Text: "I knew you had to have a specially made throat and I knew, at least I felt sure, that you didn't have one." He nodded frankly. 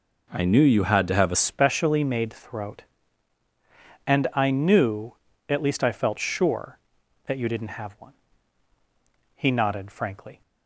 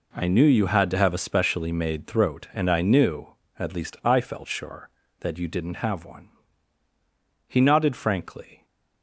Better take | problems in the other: second | changes voice at "specially"; from 1.3 s on; 9.1 s long

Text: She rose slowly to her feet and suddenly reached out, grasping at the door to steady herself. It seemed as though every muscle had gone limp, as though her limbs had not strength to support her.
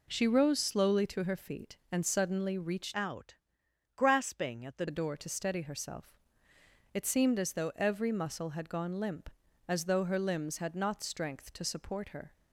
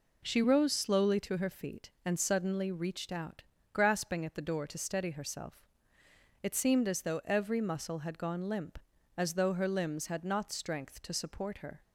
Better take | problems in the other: second | changes voice from "out" to "the"; from 2.9 to 4.8 s; 1.9 s long

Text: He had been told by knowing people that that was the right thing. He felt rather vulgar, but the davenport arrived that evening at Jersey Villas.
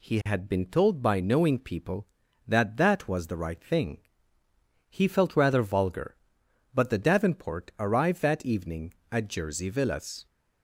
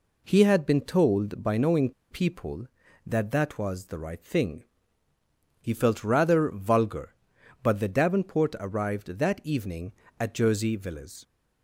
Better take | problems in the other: first | pauses between "knowing" and "people"; slight; at 1.9 s; 0.19 s long

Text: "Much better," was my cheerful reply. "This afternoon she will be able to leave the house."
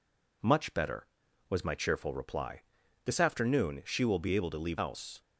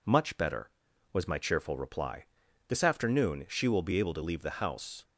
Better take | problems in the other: second | skips "the"; at 4.7 s

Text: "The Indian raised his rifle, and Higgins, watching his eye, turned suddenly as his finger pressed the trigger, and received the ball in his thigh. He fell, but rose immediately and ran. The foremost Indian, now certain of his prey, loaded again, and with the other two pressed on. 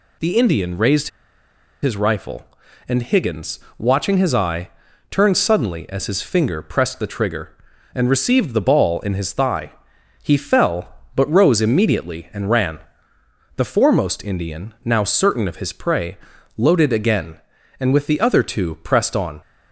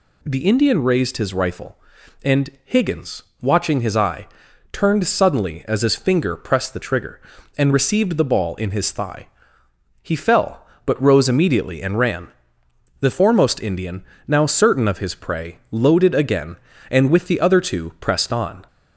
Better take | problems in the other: second | pauses between "raised" and "his"; noticeable; at 1.0 s; 0.74 s long

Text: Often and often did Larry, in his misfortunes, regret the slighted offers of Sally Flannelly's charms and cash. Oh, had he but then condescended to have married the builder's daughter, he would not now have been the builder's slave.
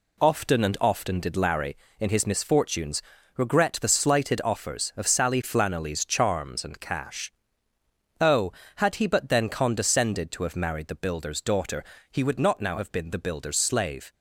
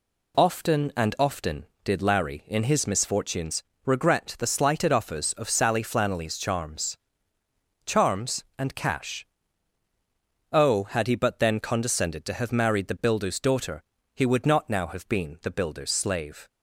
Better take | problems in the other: first | says "charms" twice; at 7.8 s

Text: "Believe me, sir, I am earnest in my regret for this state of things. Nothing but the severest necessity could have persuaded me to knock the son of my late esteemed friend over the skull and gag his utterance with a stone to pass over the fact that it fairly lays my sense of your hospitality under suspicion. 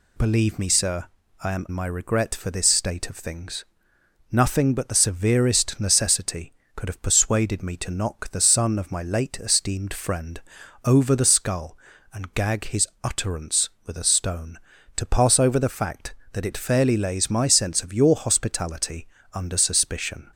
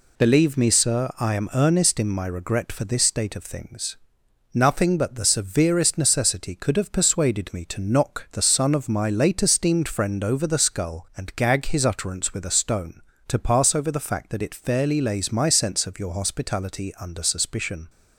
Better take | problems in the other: second | skips "earnest in"; at 1.6 s // pauses between "friend" and "over"; noticeable; at 10.3 s; 0.46 s long // pauses between "his" and "utterance"; slight; at 12.8 s; 0.16 s long // pauses between "hospitality" and "under"; slight; at 19.0 s; 0.28 s long

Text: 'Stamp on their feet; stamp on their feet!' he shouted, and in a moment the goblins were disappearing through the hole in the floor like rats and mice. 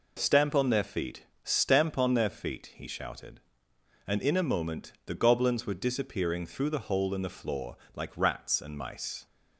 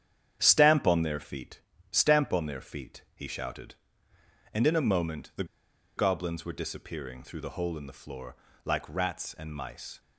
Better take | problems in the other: first | starts louder than the rest; strong; until 1.4 s; 9 dB // pauses between "the" and "goblins"; noticeable; at 5.4 s; 0.52 s long // pauses between "floor" and "like"; slight; at 8.3 s; 0.30 s long; slight in the first

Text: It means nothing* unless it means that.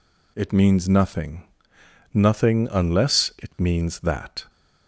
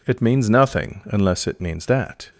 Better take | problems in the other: second | says "nothing" twice; at 2.1 s

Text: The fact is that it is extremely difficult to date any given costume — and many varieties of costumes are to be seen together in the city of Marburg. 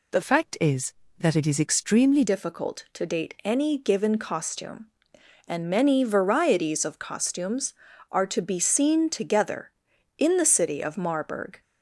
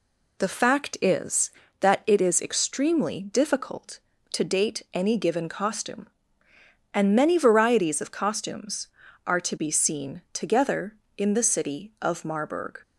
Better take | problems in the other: second | changes voice from "fact" to "extremely"; from 0.2 to 2.2 s; 2.0 s long

